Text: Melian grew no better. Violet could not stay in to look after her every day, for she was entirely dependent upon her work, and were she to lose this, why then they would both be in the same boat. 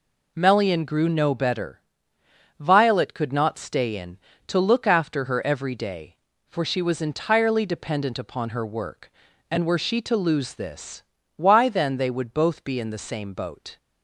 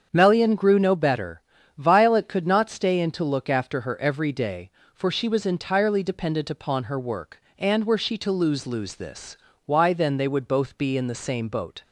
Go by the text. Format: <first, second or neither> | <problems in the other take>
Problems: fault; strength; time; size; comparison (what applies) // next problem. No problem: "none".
first | starts louder than the rest; strong; until 1.1 s; 7.5 dB // says "lose" twice; at 8.6 s